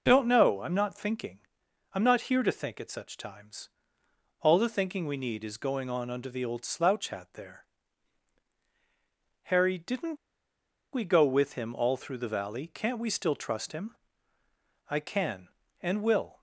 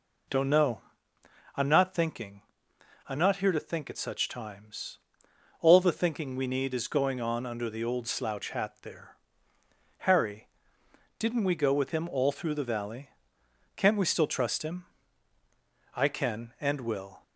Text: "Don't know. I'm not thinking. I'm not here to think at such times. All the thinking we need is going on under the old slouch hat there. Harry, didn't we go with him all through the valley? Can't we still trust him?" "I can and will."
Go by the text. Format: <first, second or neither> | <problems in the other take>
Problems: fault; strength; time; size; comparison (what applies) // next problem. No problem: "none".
second | pauses between "didn't" and "we"; noticeable; at 10.1 s; 0.76 s long